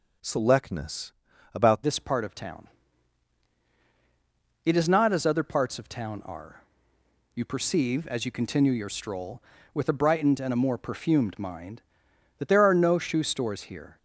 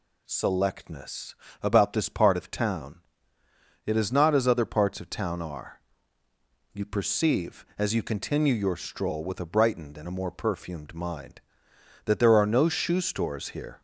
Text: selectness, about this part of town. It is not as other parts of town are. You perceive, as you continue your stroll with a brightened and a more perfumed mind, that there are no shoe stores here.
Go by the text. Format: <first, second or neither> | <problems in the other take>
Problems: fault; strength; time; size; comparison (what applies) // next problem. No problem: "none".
second | changes voice at "this"; from 1.8 s on; 12.1 s long